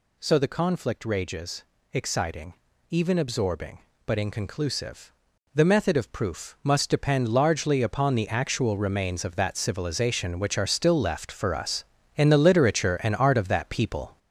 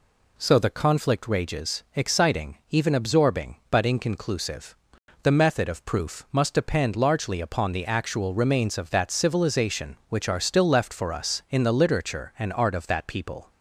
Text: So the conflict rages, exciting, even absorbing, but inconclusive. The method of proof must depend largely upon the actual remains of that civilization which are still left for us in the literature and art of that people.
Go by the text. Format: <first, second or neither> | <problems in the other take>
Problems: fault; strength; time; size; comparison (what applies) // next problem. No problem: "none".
second | gets louder; noticeable; throughout; 5.5 dB